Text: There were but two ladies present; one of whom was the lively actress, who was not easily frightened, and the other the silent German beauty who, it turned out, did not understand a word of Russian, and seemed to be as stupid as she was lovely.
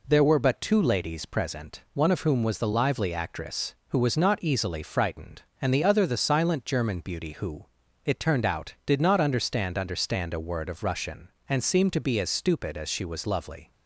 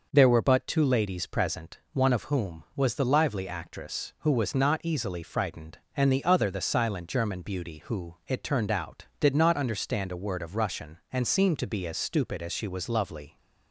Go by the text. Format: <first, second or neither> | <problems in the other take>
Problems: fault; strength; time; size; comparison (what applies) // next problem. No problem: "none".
second | says "understand" twice; at 9.7 s